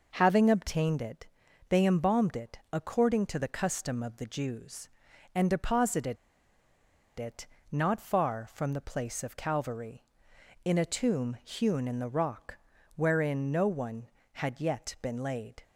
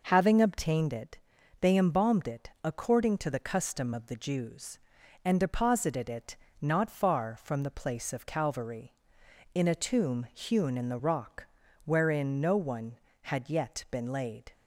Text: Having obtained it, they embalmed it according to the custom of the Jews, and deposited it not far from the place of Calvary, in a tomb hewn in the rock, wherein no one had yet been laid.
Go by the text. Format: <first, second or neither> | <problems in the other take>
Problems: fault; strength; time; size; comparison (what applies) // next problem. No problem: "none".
second | pauses between "deposited" and "it"; at 6.1 s; 1.0 s long // pauses between "it" and "not"; slight; at 7.4 s; 0.24 s long; slight in the second